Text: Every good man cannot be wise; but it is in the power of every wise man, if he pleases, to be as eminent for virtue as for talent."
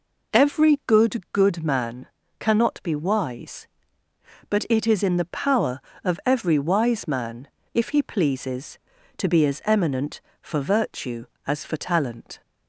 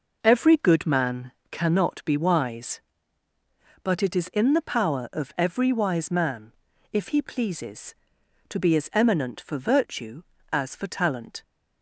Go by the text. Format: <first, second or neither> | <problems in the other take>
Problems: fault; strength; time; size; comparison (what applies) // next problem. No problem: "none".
second | says "good" twice; at 1.3 s // pauses between "man" and "cannot"; slight; at 2.0 s; 0.34 s long; slight in the second